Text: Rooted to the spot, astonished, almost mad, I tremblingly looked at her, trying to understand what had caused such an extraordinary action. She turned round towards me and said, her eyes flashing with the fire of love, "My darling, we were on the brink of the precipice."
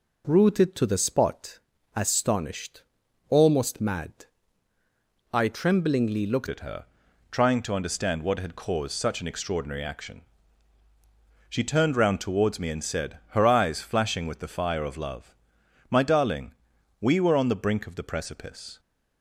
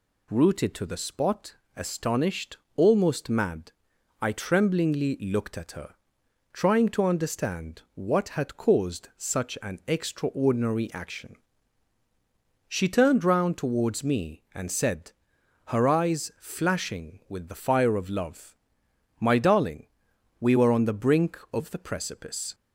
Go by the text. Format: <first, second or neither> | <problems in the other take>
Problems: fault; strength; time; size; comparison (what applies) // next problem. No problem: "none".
second | changes voice at "at"; from 6.4 s on; 12.3 s long